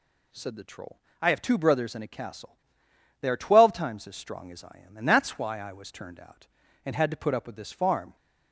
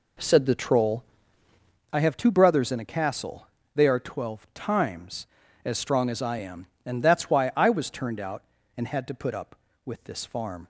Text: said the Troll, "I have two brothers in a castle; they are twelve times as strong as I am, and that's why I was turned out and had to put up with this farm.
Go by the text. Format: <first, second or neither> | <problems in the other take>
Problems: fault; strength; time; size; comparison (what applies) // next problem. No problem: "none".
first | starts louder than the rest; until 1.8 s; 3.5 dB